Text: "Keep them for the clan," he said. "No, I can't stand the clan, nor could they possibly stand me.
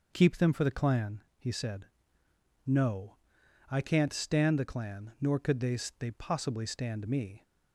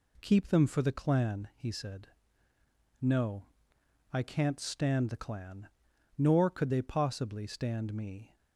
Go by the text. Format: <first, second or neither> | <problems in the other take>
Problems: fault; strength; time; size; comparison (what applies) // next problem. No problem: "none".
second | says "they" twice; at 5.9 s